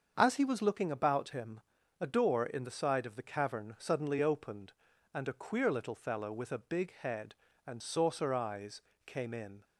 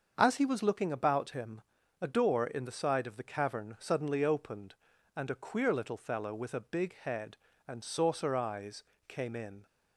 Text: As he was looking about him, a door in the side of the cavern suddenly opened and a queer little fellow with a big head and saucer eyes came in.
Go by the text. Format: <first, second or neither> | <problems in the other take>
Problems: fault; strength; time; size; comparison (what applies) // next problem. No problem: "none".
neither | starts louder than the rest; the same in both // pauses between "eyes" and "came"; slight; the same in both